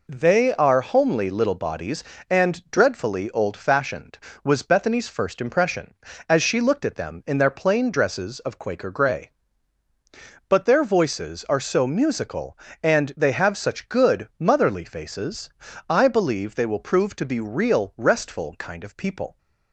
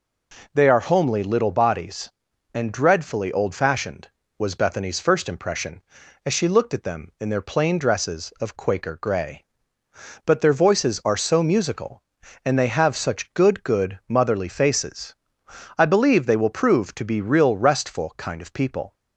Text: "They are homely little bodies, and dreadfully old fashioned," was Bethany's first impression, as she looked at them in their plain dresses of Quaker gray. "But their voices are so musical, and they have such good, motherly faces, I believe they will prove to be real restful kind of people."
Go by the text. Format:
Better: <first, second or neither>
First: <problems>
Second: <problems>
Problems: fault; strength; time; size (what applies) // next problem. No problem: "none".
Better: first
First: none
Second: says "good" twice; at 13.6 s